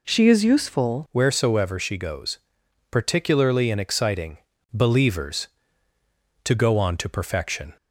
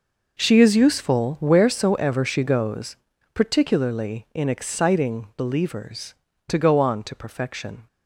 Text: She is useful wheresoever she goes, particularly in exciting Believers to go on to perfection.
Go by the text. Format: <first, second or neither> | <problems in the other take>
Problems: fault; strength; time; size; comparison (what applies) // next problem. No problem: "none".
second | changes voice at "wheresoever"; from 1.1 s on; 6.6 s long // pauses between "exciting" and "Believers"; slight; at 4.3 s; 0.34 s long